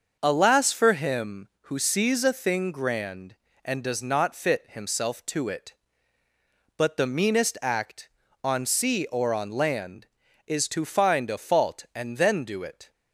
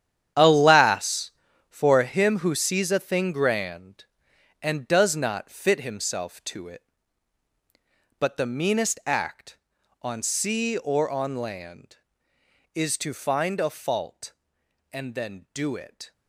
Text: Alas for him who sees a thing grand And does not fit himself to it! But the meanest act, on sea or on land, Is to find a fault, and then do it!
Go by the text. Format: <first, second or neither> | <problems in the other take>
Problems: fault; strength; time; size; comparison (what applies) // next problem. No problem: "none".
first | gets quieter; strong; throughout; 12.5 dB // starts louder than the rest; strong; until 1.7 s; 9.5 dB; also in the first